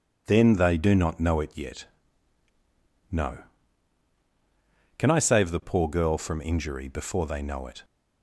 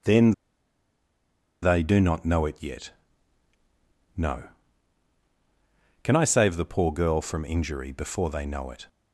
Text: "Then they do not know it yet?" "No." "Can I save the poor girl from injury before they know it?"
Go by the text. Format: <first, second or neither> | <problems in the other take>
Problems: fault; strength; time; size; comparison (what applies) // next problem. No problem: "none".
first | pauses between "Then" and "they"; strong; at 0.3 s; 1.3 s long